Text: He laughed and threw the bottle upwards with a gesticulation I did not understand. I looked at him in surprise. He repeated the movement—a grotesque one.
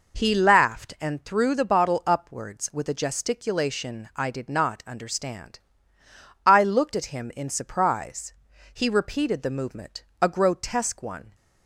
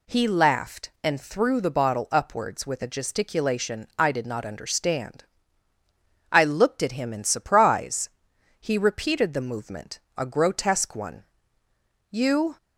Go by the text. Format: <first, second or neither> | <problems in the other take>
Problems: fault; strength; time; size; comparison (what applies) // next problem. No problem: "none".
first | goes on to say "You"; slight; from 12.1 s on; 0.46 s long